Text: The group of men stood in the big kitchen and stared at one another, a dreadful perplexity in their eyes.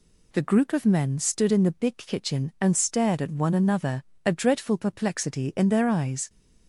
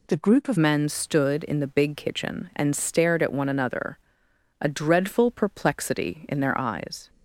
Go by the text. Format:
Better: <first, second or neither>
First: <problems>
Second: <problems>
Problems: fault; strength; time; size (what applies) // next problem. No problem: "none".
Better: first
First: none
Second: changes voice at "men"; from 0.5 s on; 6.5 s long